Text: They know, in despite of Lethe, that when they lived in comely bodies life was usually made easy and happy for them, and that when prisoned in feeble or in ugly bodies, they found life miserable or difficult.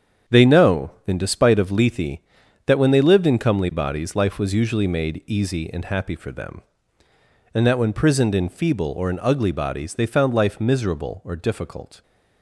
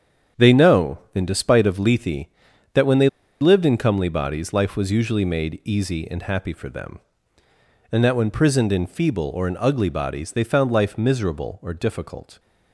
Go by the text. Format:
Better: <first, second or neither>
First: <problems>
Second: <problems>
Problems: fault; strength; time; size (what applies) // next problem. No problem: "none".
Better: first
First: starts louder than the rest; strong; until 1.4 s; 8.5 dB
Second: starts louder than the rest; strong; until 1.5 s; 8.5 dB // pauses between "they" and "lived"; slight; at 3.0 s; 0.32 s long